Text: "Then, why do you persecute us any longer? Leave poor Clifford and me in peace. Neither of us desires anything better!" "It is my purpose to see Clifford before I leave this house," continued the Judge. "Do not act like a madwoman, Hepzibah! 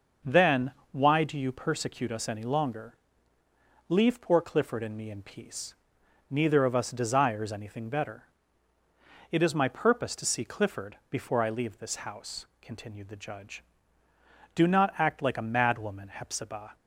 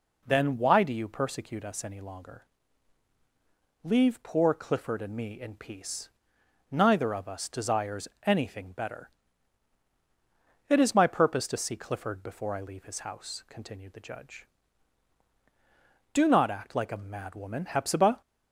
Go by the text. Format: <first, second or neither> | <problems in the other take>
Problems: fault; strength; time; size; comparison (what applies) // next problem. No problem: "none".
first | pauses between "desires" and "anything"; slight; at 8.0 s; 0.16 s long // says "his" for "this"; at 12.8 s